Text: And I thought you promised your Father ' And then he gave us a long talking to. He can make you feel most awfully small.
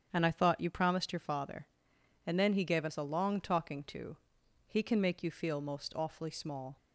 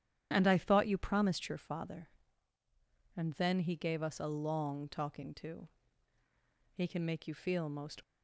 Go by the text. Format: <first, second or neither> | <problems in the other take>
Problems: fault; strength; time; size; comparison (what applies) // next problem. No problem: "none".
first | starts louder than the rest; strong; until 1.3 s; 9.5 dB; strong in the first // stops before "awfully small"; at 8.0 s